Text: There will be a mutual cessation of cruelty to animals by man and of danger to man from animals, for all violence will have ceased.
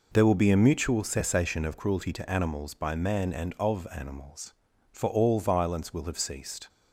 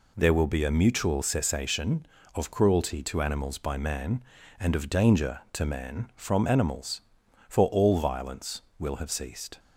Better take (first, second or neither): second